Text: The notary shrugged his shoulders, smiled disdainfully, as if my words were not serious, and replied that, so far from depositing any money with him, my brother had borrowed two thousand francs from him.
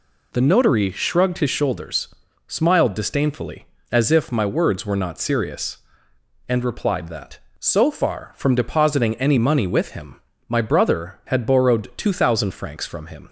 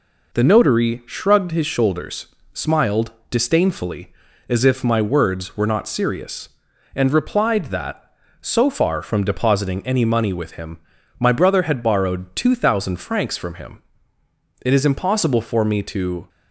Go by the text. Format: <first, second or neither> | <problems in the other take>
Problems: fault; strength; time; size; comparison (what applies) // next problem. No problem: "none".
first | pauses between "smiled" and "disdainfully"; slight; at 3.1 s; 0.18 s long // goes on to say "It is impossible for me to"; from 14.6 s on; 1.6 s long